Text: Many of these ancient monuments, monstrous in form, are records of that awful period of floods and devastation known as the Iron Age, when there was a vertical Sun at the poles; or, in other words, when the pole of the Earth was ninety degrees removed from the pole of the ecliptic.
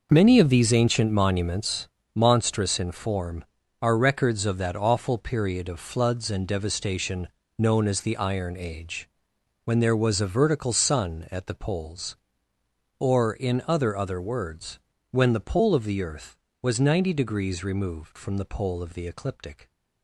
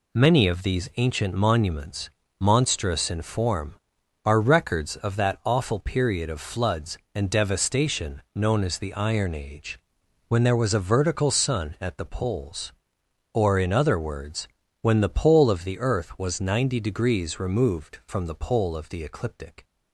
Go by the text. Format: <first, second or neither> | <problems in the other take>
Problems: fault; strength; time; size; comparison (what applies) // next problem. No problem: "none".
second | pauses between "devastation" and "known"; slight; at 7.2 s; 0.28 s long; slight in the second // says "other" twice; at 13.9 s